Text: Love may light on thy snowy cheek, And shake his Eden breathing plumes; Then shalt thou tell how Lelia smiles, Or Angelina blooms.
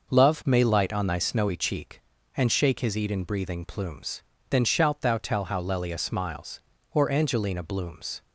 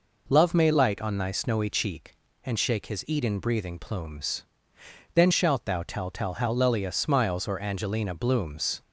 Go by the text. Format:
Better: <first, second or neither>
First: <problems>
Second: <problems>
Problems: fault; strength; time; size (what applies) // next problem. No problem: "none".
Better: first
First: none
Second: says "tell" twice; at 6.0 s